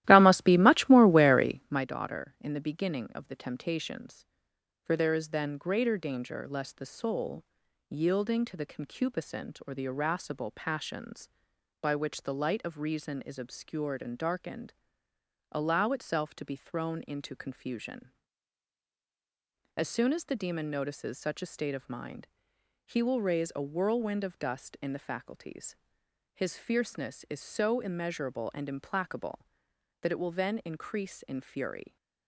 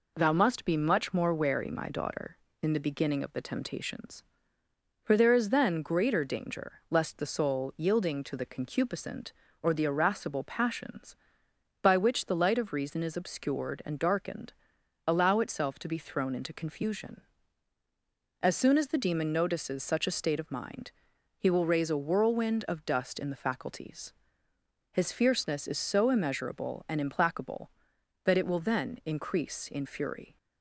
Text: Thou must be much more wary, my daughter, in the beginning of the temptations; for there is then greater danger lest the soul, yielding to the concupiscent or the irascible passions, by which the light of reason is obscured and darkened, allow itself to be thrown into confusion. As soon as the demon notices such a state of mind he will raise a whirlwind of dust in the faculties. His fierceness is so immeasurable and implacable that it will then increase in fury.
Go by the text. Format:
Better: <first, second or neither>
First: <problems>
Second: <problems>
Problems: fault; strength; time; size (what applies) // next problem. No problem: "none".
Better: second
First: starts louder than the rest; strong; until 1.8 s; 15 dB // pauses between "mind" and "he"; noticeable; at 22.2 s; 0.60 s long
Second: pauses between "mind" and "he"; noticeable; at 20.9 s; 0.48 s long